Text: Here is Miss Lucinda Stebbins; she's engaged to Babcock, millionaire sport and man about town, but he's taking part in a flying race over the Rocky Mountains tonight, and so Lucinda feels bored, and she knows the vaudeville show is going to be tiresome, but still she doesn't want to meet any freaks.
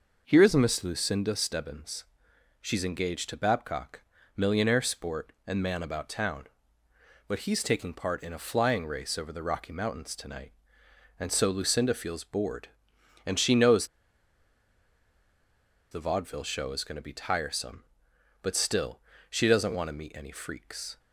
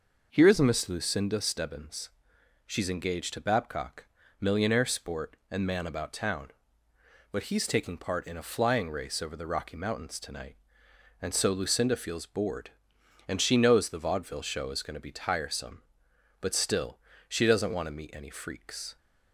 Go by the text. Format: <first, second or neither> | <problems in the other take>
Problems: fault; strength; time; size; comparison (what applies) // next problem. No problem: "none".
second | pauses between "knows" and "the"; strong; at 13.8 s; 2.0 s long // pauses between "still" and "she"; slight; at 18.9 s; 0.32 s long; slight in the second